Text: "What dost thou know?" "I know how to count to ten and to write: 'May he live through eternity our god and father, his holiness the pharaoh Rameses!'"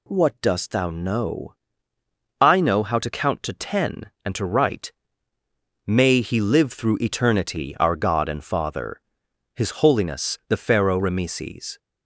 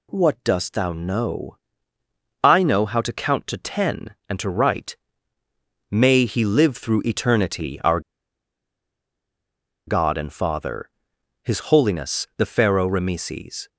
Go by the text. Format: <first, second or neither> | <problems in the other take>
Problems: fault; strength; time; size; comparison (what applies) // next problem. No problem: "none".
first | pauses between "our" and "god"; strong; at 7.9 s; 1.8 s long